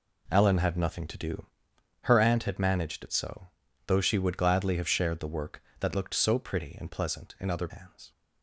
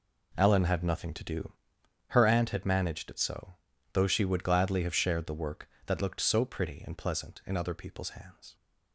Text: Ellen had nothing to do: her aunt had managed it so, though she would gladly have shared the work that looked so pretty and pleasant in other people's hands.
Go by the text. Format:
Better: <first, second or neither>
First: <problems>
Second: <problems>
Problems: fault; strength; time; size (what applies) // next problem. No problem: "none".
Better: second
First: skips "people's"; at 7.6 s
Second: none